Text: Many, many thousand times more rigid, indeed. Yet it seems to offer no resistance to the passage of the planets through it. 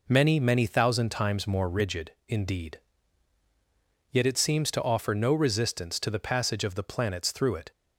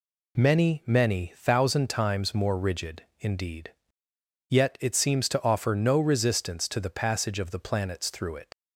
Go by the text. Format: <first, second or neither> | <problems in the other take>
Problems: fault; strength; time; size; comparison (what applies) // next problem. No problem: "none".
first | leaves "it" unfinished; at 8.5 s; 75 ms